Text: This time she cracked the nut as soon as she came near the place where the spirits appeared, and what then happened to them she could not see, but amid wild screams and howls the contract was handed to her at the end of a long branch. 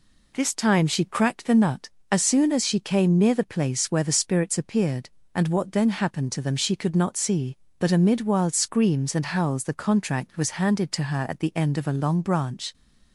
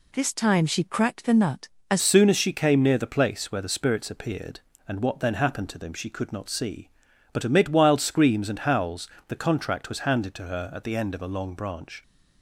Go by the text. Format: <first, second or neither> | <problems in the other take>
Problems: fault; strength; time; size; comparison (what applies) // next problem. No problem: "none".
first | changes voice at "soon"; from 2.0 s on; 10.0 s long // pauses between "howls" and "the"; slight; at 9.1 s; 0.18 s long